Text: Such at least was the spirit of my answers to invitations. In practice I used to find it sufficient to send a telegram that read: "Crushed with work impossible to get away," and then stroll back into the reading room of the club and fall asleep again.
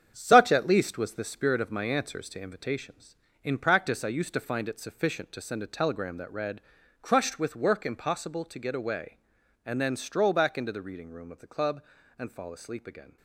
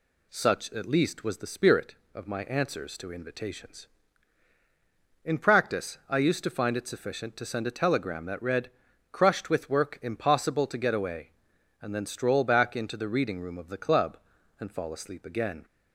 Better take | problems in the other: second | gets quieter; strong; throughout; 7.5 dB

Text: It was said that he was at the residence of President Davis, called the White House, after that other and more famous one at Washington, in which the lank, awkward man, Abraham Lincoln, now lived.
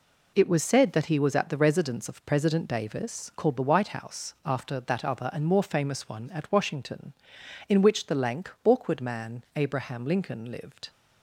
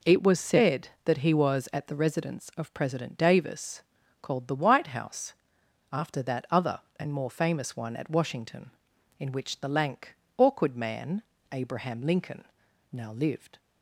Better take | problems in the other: second | skips "now"; at 10.5 s

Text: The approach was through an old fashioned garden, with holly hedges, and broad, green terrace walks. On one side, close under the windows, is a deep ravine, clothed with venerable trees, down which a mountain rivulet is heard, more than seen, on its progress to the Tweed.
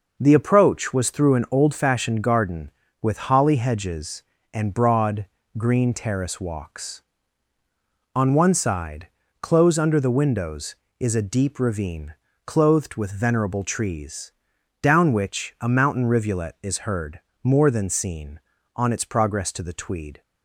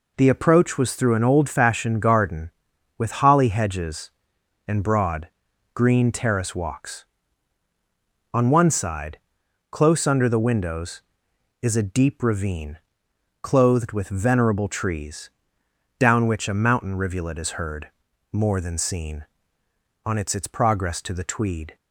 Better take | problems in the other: first | says "its" twice; at 20.3 s

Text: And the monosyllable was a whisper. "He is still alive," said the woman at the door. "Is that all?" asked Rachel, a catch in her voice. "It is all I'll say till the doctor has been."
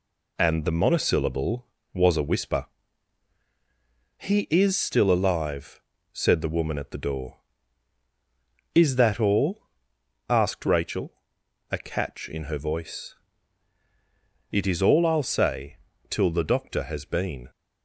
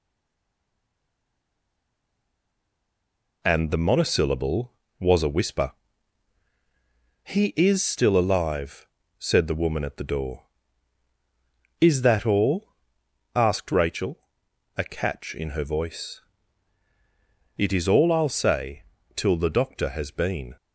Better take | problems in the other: first | stays silent before the first word; strong; until 3.4 s; 3.4 s long // pauses between "say" and "till"; slight; at 18.8 s; 0.34 s long; slight in the first

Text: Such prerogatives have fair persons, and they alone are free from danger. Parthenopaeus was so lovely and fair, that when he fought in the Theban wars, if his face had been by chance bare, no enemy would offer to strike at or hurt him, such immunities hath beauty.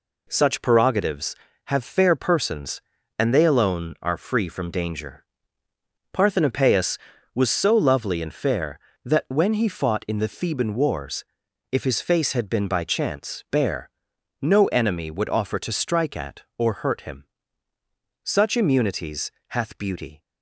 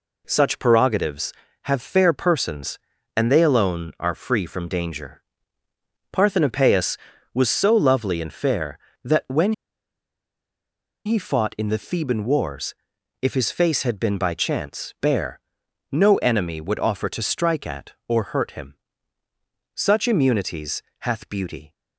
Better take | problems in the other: first | pauses between "when" and "he"; strong; at 9.5 s; 1.5 s long // pauses between "immunities" and "hath"; slight; at 20.8 s; 0.20 s long; slight in the first

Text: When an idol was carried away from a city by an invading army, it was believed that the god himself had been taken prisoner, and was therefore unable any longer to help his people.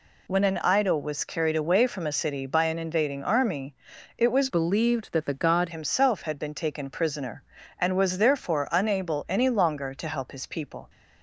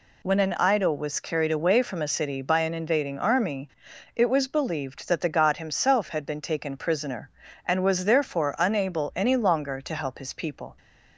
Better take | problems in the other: second | changes voice from "believed" to "god"; from 4.4 to 5.6 s; 1.2 s long

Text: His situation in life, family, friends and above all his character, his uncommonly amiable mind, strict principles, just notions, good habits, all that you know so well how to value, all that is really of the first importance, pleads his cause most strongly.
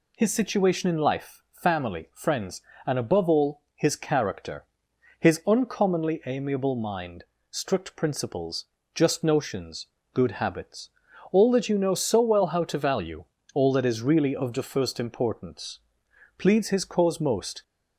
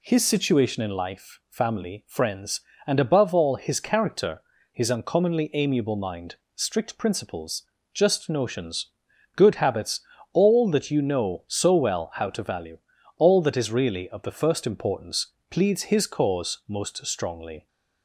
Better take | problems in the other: second | stops before "strongly"; at 17.6 s

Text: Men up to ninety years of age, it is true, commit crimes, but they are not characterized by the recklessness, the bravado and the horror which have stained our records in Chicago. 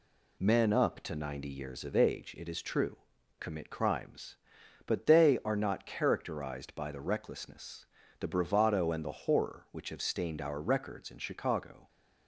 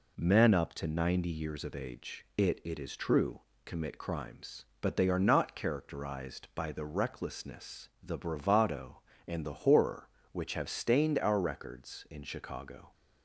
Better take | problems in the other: first | says "it" twice; at 2.6 s

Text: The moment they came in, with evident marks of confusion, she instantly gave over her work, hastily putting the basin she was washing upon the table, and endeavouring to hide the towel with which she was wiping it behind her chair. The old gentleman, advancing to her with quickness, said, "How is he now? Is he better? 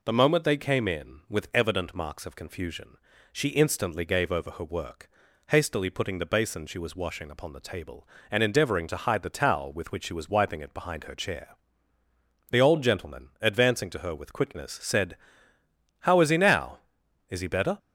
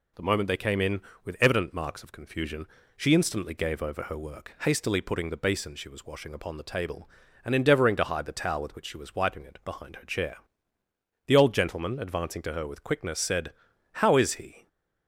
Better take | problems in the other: first | stops before "now Is he better"; at 14.6 s

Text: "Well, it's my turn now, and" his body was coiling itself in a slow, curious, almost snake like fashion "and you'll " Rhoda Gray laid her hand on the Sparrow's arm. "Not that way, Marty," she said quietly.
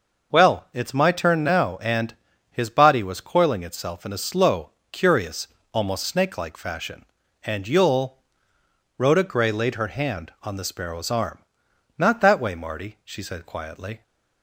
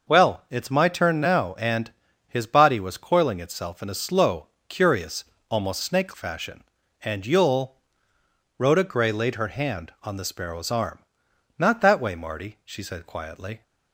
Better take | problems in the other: first | pauses between "and" and "his"; at 1.9 s; 0.38 s long; also in the first // skips "like"; at 6.1 s

